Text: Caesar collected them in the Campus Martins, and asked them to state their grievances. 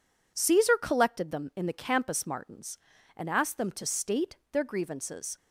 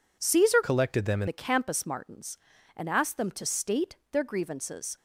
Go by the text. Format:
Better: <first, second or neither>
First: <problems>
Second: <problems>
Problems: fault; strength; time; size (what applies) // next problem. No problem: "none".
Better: first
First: pauses between "state" and "their"; slight; at 4.3 s; 0.16 s long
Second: changes voice from "collected" to "in"; from 0.6 to 1.2 s; 0.6 s long // pauses between "state" and "their"; slight; at 3.9 s; 0.16 s long